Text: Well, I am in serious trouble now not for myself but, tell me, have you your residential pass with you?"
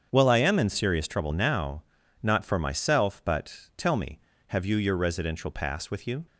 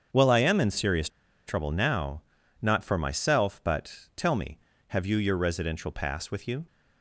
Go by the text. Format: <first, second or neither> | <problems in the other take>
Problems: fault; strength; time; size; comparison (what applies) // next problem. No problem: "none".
first | starts louder than the rest; strong; until 1.5 s; 7.5 dB; strong in the first // pauses between "serious" and "trouble"; at 1.0 s; 0.37 s long // pauses between "now" and "not"; at 2.2 s; 0.40 s long; also in the first